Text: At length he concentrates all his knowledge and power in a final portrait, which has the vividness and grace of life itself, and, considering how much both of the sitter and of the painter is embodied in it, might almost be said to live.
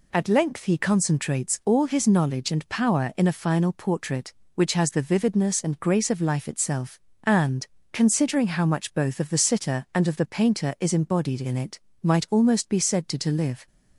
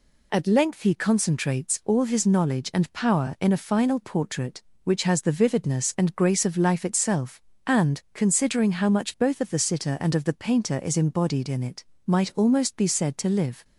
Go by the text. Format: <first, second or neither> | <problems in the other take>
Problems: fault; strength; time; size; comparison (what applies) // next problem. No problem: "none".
second | says "to" twice; at 13.1 s